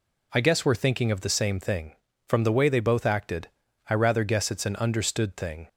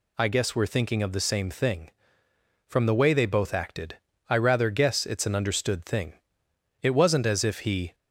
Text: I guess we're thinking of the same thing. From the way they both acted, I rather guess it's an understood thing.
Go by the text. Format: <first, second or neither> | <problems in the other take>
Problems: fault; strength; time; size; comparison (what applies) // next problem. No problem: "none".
first | goes on to say "It wasn't as if he"; noticeable; from 6.8 s on; 1.1 s long